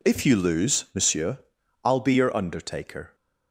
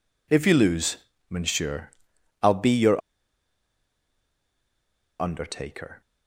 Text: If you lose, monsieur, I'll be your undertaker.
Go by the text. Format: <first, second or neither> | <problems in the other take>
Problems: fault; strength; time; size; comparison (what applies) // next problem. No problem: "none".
first | pauses between "your" and "undertaker"; strong; at 2.9 s; 2.1 s long